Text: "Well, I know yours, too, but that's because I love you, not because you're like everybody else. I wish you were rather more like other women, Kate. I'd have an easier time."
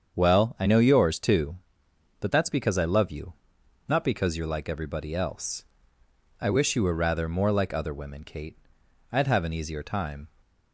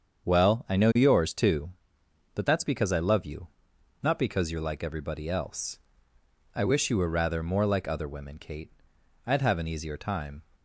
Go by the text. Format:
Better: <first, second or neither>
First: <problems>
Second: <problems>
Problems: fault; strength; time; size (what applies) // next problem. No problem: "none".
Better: neither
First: starts louder than the rest; strong; until 1.2 s; 7 dB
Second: starts louder than the rest; until 1.3 s; 7 dB